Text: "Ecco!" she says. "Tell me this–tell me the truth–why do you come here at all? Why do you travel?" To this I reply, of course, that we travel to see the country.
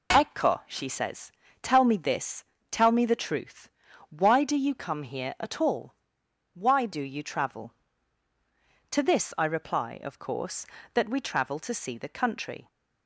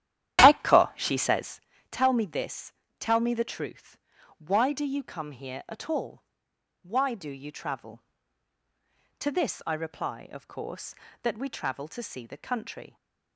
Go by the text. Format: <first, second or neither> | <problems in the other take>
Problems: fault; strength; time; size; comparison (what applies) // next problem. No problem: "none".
first | starts louder than the rest; strong; until 1.7 s; 11.5 dB